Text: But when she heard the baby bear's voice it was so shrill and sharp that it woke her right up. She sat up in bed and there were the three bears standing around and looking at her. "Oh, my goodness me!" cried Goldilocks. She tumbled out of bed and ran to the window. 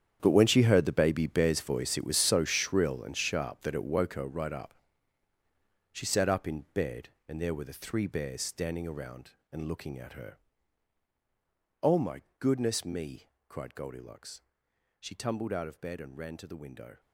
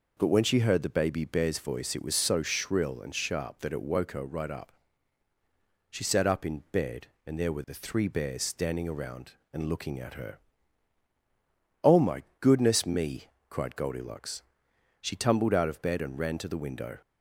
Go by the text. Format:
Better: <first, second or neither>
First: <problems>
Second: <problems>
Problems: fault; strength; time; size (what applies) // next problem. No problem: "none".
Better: second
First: gets quieter; strong; throughout; 15 dB // pauses between "my" and "goodness"; slight; at 12.2 s; 0.16 s long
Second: pauses between "my" and "goodness"; slight; at 12.2 s; 0.16 s long